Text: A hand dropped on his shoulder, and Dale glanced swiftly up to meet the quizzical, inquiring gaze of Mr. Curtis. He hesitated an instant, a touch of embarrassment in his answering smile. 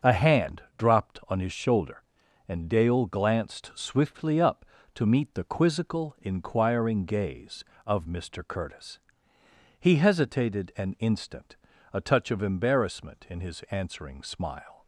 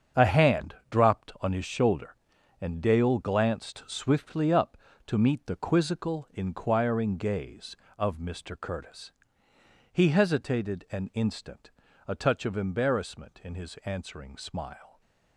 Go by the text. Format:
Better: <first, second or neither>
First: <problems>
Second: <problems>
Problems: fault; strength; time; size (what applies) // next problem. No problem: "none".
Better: first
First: starts louder than the rest; noticeable; until 1.2 s; 6 dB // pauses between "hand" and "dropped"; slight; at 0.6 s; 0.16 s long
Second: gets quieter; strong; throughout; 10.5 dB // starts louder than the rest; strong; until 1.3 s; 7.5 dB // pauses between "hand" and "dropped"; slight; at 0.7 s; 0.16 s long